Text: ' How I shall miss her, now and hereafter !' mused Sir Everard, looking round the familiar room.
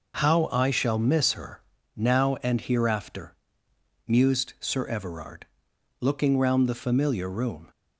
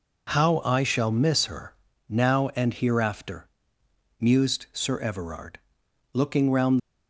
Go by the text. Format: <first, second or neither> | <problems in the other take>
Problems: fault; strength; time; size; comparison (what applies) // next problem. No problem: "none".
first | stops before "the familiar room"; at 6.7 s